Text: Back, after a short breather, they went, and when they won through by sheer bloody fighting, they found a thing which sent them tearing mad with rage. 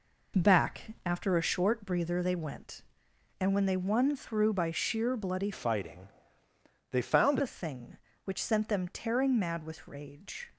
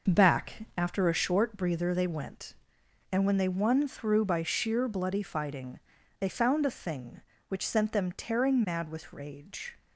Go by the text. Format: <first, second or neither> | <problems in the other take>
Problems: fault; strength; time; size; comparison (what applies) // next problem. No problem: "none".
second | changes voice from "fighting" to "found"; from 5.5 to 7.3 s; 1.8 s long